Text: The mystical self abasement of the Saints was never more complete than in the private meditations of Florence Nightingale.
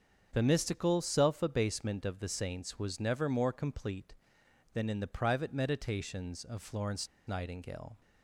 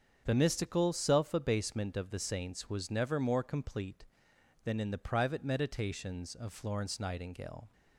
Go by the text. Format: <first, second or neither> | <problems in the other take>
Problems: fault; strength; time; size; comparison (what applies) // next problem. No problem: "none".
second | starts louder than the rest; strong; until 1.3 s; 7 dB; strong in the second // pauses between "Florence" and "Nightingale"; slight; at 7.0 s; 0.20 s long